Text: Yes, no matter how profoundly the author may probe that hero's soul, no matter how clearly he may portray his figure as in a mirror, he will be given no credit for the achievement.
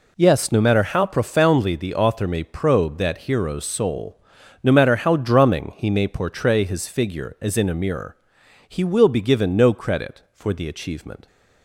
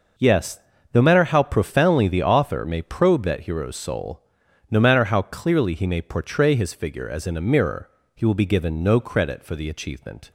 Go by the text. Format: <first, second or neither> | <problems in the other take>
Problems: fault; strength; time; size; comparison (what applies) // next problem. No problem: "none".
second | says "drumming" for "clearly"; at 5.1 s